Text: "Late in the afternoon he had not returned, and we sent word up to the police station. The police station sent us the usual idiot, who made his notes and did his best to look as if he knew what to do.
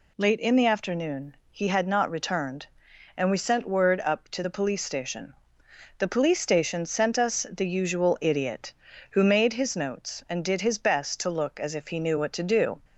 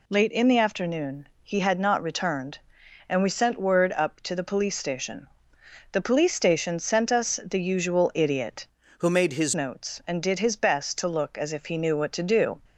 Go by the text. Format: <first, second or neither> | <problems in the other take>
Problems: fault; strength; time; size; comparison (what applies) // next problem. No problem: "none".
first | changes voice from "who" to "his"; from 8.9 to 9.5 s; 0.6 s long